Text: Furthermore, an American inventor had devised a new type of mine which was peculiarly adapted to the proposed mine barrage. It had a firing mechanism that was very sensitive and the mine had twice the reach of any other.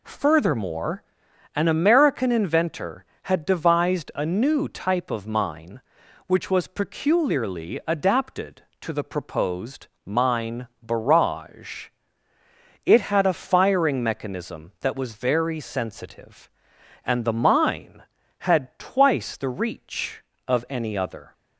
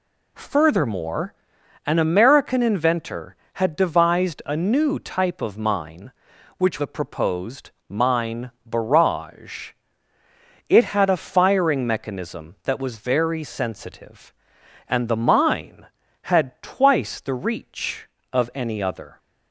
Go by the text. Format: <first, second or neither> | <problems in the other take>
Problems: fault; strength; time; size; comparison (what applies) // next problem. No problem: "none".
first | skips "was peculiarly adapted to"; at 6.7 s // pauses between "proposed" and "mine"; slight; at 7.6 s; 0.18 s long; slight in the first // pauses between "mine" and "barrage"; slight; at 8.4 s; 0.16 s long; slight in the first